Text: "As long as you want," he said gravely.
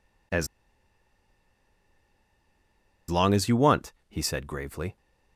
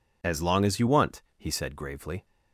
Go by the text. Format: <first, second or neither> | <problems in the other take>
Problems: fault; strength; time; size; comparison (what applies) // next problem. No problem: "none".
second | pauses between "As" and "long"; strong; at 0.4 s; 2.6 s long